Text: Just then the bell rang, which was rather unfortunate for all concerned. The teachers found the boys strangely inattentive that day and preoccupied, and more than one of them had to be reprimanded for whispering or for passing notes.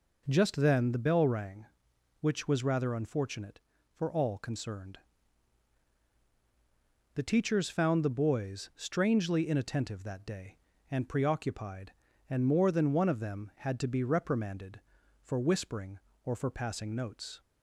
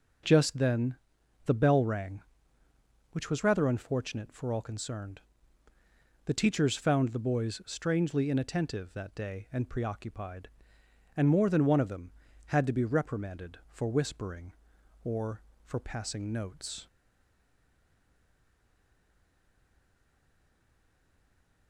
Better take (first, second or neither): first